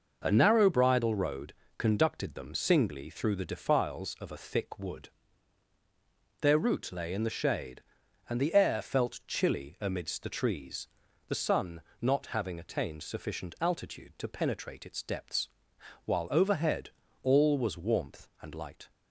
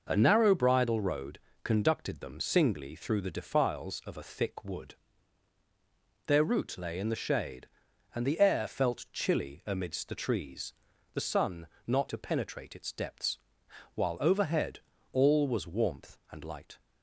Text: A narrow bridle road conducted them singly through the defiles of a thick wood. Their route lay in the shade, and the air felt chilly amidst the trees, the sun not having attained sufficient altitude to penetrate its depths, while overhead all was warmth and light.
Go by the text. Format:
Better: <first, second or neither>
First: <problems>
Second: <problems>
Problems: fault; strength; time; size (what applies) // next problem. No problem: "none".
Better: first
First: pauses between "road" and "conducted"; slight; at 1.5 s; 0.26 s long // pauses between "sun" and "not"; slight; at 11.8 s; 0.18 s long // pauses between "overhead" and "all"; slight; at 16.9 s; 0.34 s long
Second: pauses between "road" and "conducted"; slight; at 1.3 s; 0.26 s long // pauses between "sun" and "not"; slight; at 11.6 s; 0.18 s long // skips "having attained sufficient altitude"; at 12.0 s // pauses between "overhead" and "all"; slight; at 14.7 s; 0.34 s long